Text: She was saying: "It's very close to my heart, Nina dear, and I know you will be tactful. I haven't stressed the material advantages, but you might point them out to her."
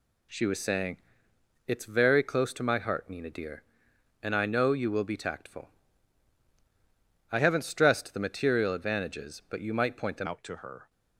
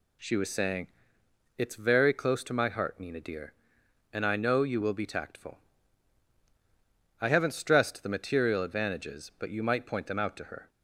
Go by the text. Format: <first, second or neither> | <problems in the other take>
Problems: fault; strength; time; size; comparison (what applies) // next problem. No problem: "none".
second | changes voice at "out"; from 10.2 s on; 0.6 s long